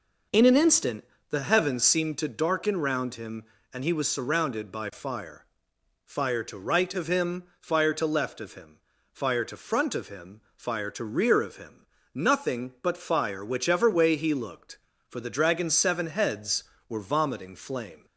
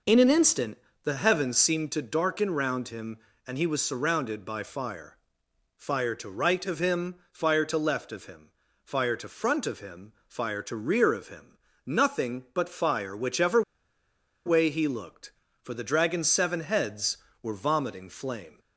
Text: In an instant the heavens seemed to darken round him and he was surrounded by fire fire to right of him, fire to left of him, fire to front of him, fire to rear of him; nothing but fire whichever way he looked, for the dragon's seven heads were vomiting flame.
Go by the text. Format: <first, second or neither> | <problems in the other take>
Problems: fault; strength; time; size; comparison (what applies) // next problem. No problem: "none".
first | pauses between "instant" and "the"; slight; at 0.7 s; 0.28 s long; slight in the first // pauses between "fire" and "fire"; noticeable; at 5.1 s; 0.60 s long; noticeable in the first // pauses between "whichever" and "way"; noticeable; at 13.6 s; 0.84 s long